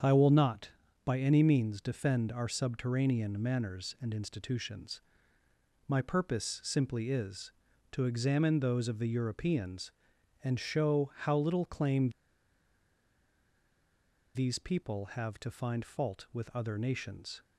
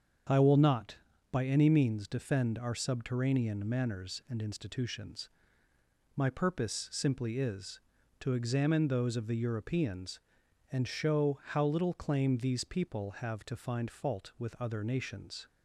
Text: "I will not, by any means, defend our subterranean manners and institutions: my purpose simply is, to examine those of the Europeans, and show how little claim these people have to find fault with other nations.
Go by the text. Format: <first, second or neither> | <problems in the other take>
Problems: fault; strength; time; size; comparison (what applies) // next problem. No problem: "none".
second | starts louder than the rest; strong; until 1.3 s; 7.5 dB; strong in the second // pauses between "claim" and "these"; strong; at 12.0 s; 2.2 s long